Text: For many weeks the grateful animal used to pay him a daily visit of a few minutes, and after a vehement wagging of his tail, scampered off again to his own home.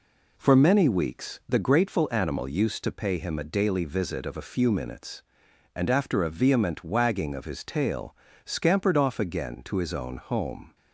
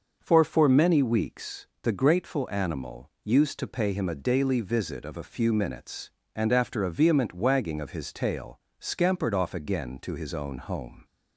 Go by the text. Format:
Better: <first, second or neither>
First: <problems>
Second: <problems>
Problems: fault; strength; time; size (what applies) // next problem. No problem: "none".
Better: first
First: none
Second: starts louder than the rest; until 1.2 s; 6 dB // says "For" twice; at 0.4 s // pauses between "weeks" and "the"; slight; at 1.6 s; 0.16 s long